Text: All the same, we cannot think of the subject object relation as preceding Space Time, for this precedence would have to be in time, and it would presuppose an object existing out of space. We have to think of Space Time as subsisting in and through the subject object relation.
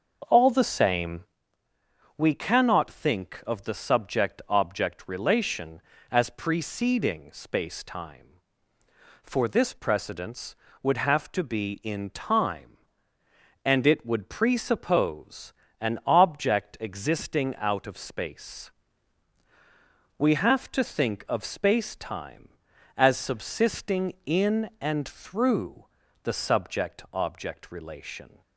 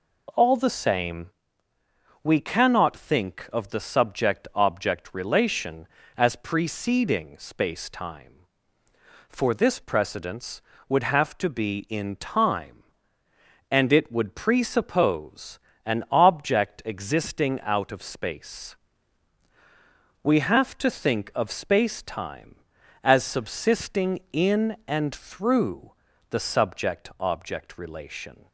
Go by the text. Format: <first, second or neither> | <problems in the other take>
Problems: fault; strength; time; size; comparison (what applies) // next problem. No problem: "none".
second | starts louder than the rest; until 1.4 s; 6.5 dB // pauses between "presuppose" and "an"; slight; at 15.5 s; 0.28 s long; slight in the second // pauses between "through" and "the"; at 25.8 s; 0.38 s long; also in the second